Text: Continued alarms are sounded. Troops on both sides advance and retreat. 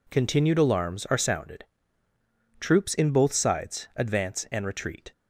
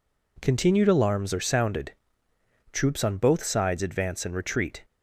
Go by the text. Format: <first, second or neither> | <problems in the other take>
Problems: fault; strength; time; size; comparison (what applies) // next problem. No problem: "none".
second | says "in" for "on"; at 2.9 s